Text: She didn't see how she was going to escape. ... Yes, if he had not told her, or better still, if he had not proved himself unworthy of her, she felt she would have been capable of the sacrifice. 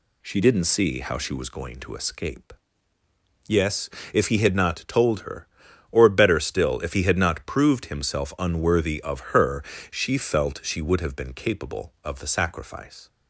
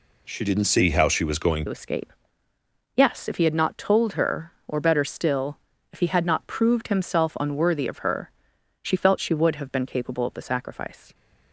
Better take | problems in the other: first | changes voice at "to"; from 1.6 s on; 9.5 s long

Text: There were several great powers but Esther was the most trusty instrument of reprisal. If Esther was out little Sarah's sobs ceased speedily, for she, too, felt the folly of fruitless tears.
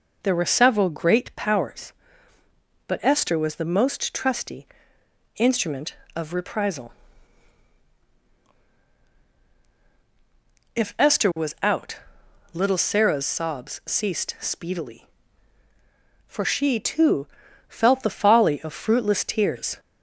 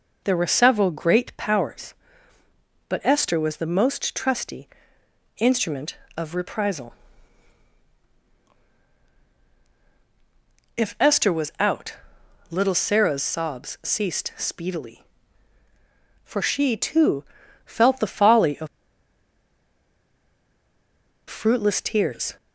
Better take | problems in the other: first | pauses between "trusty" and "instrument"; noticeable; at 4.6 s; 0.70 s long; noticeable in the first // pauses between "out" and "little"; noticeable; at 11.9 s; 0.54 s long; noticeable in the first // pauses between "of" and "fruitless"; strong; at 18.6 s; 2.6 s long

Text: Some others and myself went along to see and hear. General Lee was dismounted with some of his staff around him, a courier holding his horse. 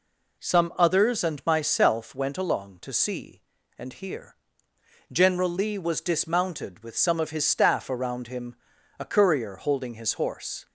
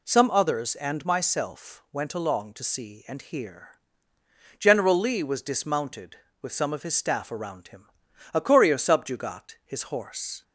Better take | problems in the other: first | says "subjugat" for "holding"; at 8.7 s

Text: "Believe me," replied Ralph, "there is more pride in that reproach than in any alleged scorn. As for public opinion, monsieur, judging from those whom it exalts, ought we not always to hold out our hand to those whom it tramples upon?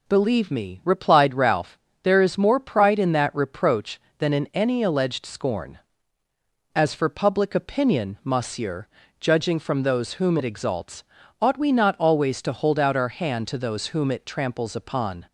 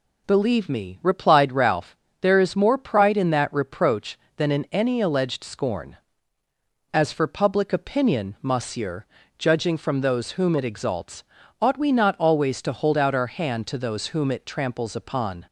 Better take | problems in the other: neither | none

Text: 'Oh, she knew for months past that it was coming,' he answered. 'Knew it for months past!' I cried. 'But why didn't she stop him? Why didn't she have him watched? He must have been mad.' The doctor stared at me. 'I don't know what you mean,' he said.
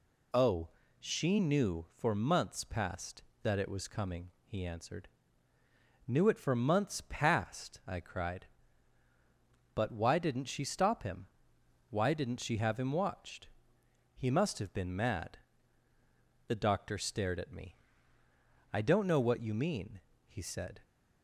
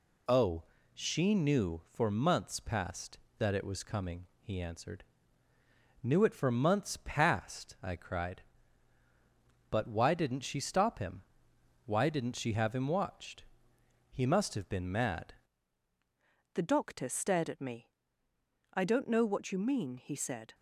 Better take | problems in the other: first | changes voice at "The"; from 16.5 s on; 4.0 s long

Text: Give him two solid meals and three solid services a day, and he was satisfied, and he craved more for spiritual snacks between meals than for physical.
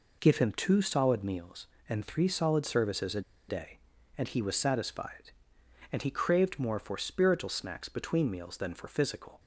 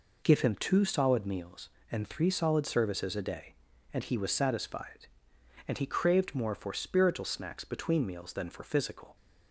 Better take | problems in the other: second | pauses between "a" and "day"; slight; at 3.2 s; 0.27 s long

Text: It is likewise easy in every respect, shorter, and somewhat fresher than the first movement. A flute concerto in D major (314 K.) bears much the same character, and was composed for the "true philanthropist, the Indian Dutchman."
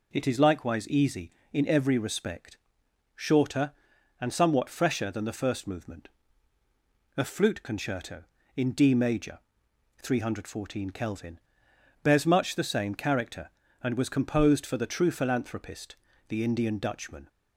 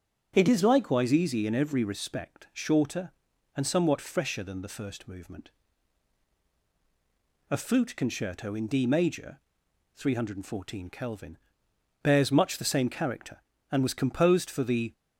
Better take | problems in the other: first | starts louder than the rest; strong; until 1.3 s; 8 dB // stops before "true philanthropist the Indian Dutchman"; at 14.9 s

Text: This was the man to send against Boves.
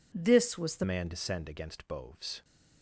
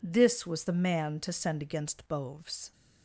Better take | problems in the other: second | changes voice at "man"; from 0.8 s on; 1.6 s long

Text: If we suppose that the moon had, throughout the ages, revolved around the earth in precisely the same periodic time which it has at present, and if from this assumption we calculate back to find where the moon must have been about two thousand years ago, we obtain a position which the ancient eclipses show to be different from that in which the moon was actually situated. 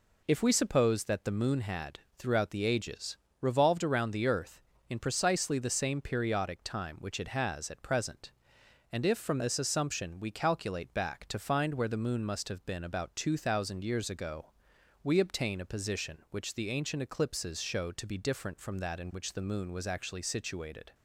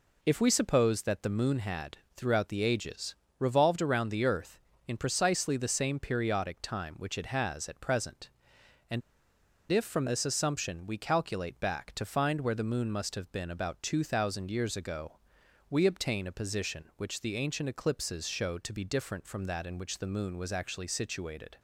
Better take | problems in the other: first | pauses between "and" and "if"; noticeable; at 9.0 s; 0.70 s long

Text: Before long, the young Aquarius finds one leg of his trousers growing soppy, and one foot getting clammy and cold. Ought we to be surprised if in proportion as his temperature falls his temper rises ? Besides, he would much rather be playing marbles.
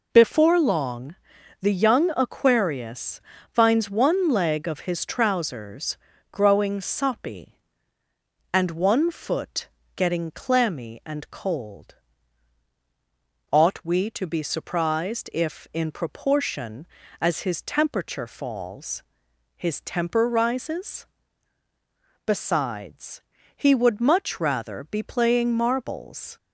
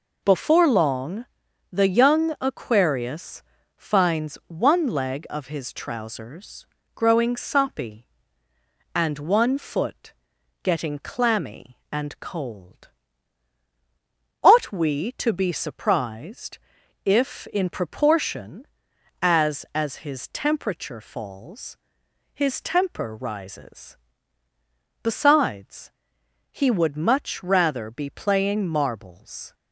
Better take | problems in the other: first | pauses between "Aquarius" and "finds"; slight; at 3.4 s; 0.34 s long; slight in the first // pauses between "trousers" and "growing"; slight; at 6.6 s; 0.28 s long; slight in the first // pauses between "foot" and "getting"; noticeable; at 10.1 s; 0.50 s long; slight in the first // pauses between "surprised" and "if"; noticeable; at 16.5 s; 0.48 s long // says "as" twice; at 19.7 s // pauses between "falls" and "his"; noticeable; at 21.7 s; 0.56 s long; noticeable in the first

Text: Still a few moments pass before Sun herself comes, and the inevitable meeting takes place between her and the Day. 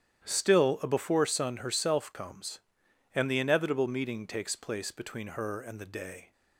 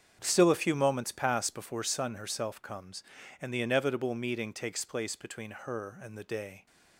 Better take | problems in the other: second | starts louder than the rest; strong; until 1.3 s; 11 dB; strong in the second // skips "few moments pass"; at 0.8 s

